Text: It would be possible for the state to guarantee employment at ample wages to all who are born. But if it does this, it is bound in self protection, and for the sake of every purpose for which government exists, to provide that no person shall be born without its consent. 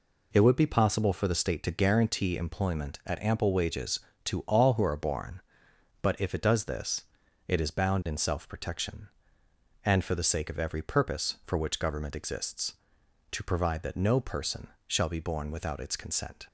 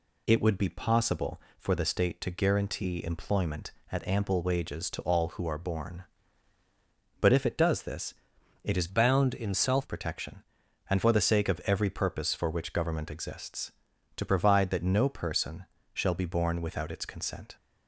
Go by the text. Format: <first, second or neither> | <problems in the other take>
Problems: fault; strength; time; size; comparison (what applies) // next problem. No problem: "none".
first | changes voice from "bound" to "self"; from 8.8 to 9.8 s; 1.0 s long // pauses between "person" and "shall"; slight; at 15.6 s; 0.28 s long; slight in the first